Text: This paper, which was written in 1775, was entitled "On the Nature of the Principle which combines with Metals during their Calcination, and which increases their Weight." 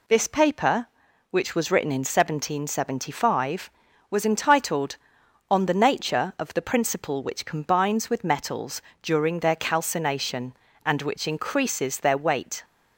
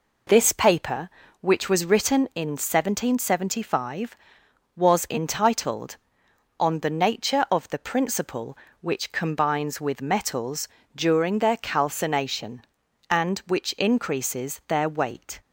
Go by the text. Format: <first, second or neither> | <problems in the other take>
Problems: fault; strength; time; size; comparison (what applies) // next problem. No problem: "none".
neither | pauses between "Metals" and "during"; slight; the same in both